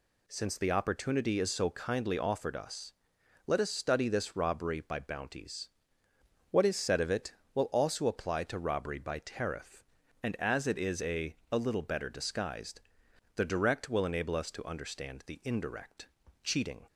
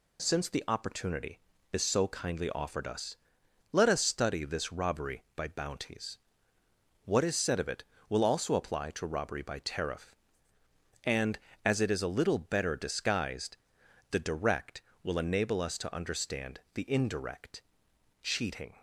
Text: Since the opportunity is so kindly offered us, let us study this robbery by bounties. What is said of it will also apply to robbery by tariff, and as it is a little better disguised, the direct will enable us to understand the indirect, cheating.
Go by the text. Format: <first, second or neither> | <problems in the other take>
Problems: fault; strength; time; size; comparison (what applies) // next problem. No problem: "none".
second | says "a" twice; at 11.5 s